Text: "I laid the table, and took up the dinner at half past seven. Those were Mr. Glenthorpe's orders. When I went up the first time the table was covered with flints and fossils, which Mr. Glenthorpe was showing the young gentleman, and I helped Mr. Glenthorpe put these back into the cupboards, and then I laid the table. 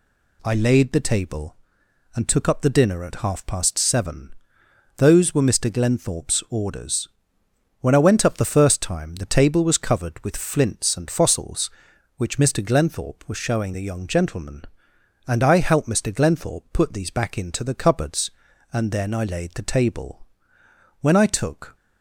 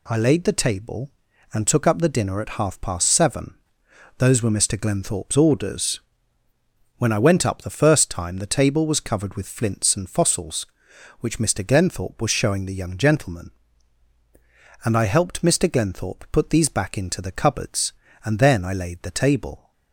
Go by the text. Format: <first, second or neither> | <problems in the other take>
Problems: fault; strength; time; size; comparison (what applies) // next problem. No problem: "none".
second | goes on to say "When I took"; noticeable; from 21.0 s on; 0.74 s long